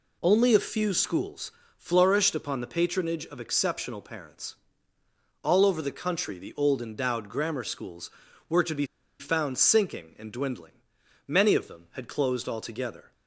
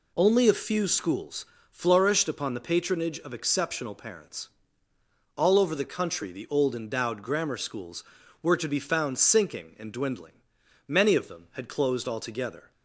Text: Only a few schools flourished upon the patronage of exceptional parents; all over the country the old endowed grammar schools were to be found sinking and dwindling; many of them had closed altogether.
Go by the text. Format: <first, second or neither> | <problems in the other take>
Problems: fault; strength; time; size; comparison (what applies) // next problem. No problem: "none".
second | pauses between "schools" and "flourished"; slight; at 1.5 s; 0.24 s long; slight in the second // pauses between "be" and "found"; slight; at 8.8 s; 0.34 s long